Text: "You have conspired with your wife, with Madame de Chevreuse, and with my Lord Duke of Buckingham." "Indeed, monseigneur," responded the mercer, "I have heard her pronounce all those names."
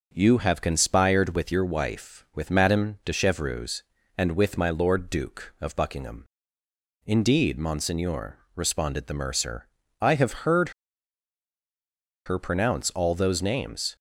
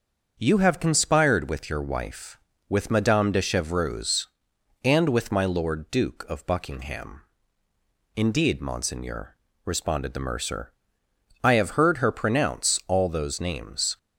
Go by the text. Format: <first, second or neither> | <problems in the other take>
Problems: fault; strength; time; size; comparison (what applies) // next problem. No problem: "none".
second | starts louder than the rest; until 1.1 s; 6.5 dB; also in the second // pauses between "heard" and "her"; strong; at 10.7 s; 1.5 s long